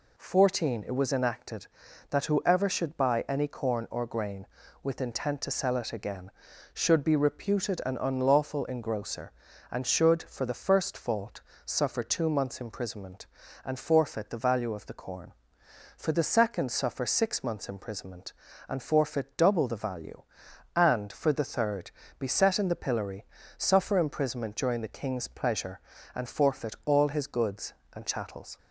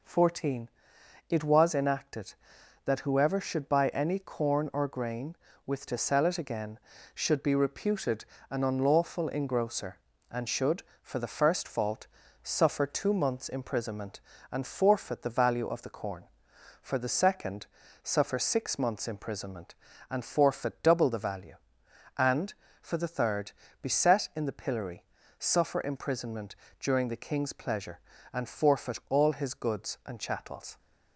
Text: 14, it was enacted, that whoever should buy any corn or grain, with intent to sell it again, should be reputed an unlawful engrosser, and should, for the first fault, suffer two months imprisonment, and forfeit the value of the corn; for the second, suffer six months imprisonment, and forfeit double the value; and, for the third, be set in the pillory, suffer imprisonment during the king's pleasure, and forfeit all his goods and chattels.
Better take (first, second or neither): first